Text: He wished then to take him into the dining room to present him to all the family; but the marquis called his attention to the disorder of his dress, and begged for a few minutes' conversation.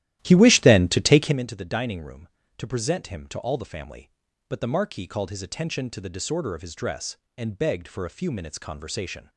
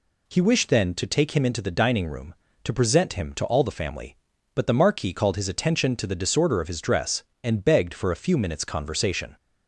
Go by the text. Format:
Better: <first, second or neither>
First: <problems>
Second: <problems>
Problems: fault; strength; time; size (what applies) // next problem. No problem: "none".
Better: second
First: starts louder than the rest; strong; until 1.4 s; 14 dB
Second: none